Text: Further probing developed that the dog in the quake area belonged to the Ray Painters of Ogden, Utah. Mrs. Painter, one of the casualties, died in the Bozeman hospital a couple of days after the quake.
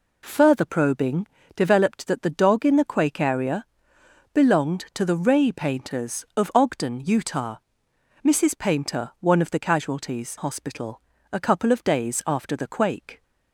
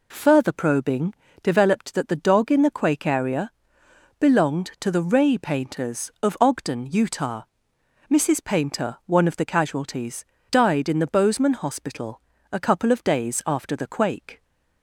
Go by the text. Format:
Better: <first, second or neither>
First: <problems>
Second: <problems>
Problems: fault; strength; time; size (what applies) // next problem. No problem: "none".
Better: second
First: pauses between "probing" and "developed"; slight; at 1.2 s; 0.26 s long // pauses between "area" and "belonged"; noticeable; at 3.6 s; 0.68 s long // skips "died in the Bozeman"; at 10.3 s // pauses between "hospital" and "a"; slight; at 11.0 s; 0.32 s long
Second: pauses between "probing" and "developed"; slight; at 1.1 s; 0.26 s long // pauses between "area" and "belonged"; noticeable; at 3.5 s; 0.68 s long // pauses between "hospital" and "a"; slight; at 12.2 s; 0.32 s long